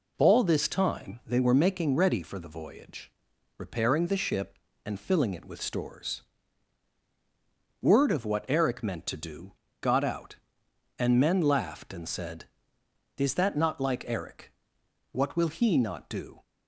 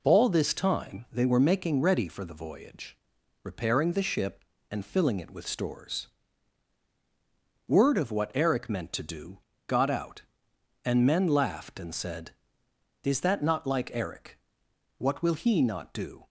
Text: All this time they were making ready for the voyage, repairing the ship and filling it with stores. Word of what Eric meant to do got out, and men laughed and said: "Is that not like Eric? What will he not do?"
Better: neither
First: pauses between "do" and "got"; slight; at 9.5 s; 0.28 s long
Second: pauses between "do" and "got"; slight; at 9.3 s; 0.28 s long

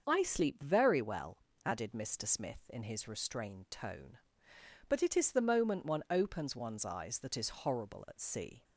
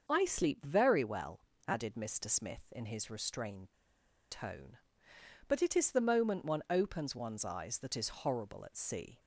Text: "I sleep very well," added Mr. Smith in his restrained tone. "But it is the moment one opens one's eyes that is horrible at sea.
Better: first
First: starts louder than the rest; until 1.0 s; 6.5 dB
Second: starts louder than the rest; until 1.0 s; 6.5 dB // pauses between "restrained" and "tone"; noticeable; at 3.7 s; 0.58 s long

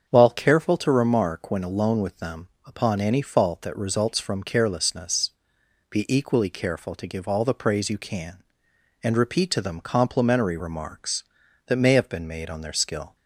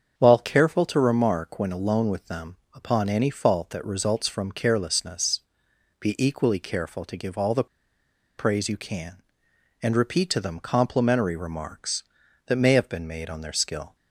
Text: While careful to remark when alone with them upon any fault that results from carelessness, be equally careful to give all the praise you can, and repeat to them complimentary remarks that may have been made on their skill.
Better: first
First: starts louder than the rest; strong; until 1.1 s; 7 dB // pauses between "them" and "upon"; slight; at 2.4 s; 0.18 s long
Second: starts louder than the rest; strong; until 1.1 s; 7 dB // pauses between "them" and "upon"; slight; at 2.5 s; 0.18 s long // pauses between "the" and "praise"; noticeable; at 7.6 s; 0.71 s long

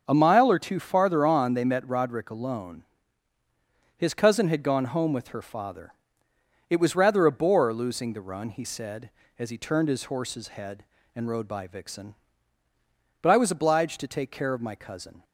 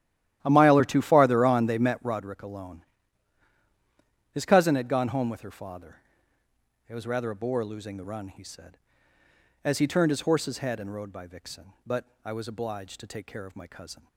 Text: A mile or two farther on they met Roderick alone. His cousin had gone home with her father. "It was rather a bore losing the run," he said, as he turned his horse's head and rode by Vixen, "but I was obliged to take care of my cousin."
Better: first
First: none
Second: starts louder than the rest; strong; until 2.3 s; 12.5 dB // pauses between "but" and "I"; slight; at 12.0 s; 0.18 s long

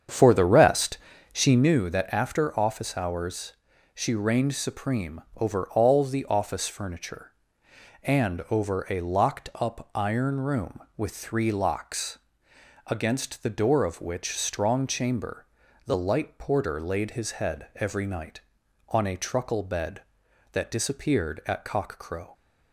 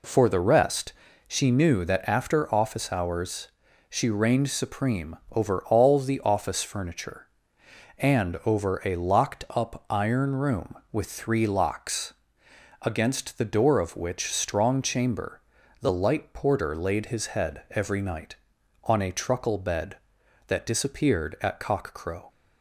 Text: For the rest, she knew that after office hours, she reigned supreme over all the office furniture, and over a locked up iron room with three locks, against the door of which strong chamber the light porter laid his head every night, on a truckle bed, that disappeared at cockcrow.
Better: second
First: starts louder than the rest; strong; until 1.7 s; 8 dB // pauses between "chamber" and "the"; at 15.4 s; 0.40 s long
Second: pauses between "chamber" and "the"; at 15.4 s; 0.40 s long

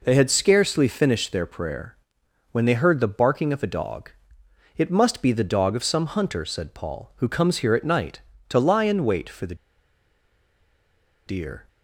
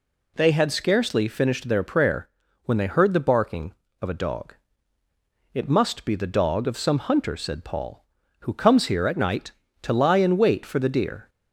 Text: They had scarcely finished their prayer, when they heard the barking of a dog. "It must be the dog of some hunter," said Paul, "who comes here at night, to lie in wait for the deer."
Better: second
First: pauses between "the" and "deer"; strong; at 9.5 s; 1.7 s long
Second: none

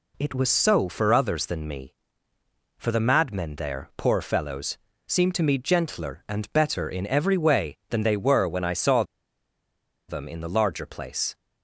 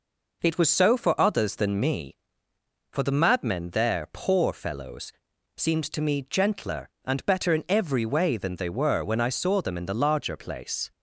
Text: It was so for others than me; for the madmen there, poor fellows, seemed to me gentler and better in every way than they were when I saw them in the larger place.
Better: second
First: pauses between "saw" and "them"; at 9.0 s; 1.0 s long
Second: none

